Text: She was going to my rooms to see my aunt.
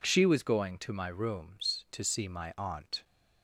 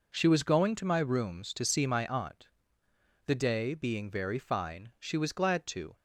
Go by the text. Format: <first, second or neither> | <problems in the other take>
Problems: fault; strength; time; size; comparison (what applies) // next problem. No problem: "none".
first | goes on to say "The day being very fine she was glad to"; strong; from 3.2 s on; 2.7 s long